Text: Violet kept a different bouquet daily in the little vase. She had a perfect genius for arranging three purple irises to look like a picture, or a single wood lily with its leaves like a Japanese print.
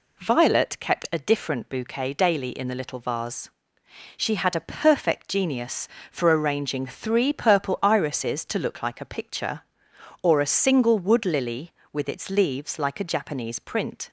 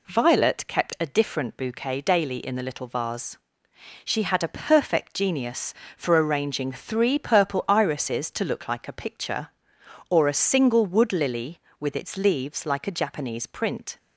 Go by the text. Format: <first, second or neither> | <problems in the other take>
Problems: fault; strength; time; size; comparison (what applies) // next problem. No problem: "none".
neither | none